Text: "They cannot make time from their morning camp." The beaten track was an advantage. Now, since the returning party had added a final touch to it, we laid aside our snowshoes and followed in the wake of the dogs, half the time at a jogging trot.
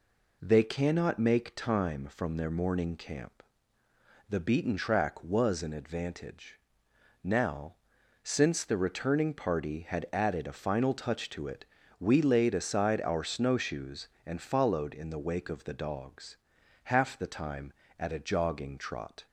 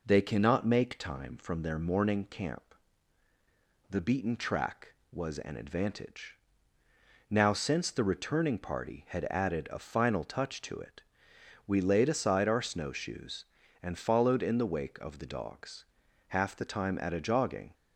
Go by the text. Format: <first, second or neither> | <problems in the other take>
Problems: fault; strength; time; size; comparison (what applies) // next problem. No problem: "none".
first | stops before "trot"; at 17.7 s